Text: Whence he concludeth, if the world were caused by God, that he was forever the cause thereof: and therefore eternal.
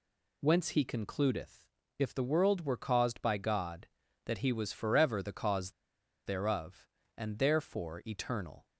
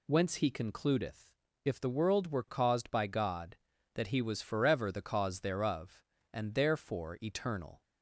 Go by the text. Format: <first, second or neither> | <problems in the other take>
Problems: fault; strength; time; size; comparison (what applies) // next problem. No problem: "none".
second | pauses between "cause" and "thereof"; noticeable; at 5.6 s; 0.56 s long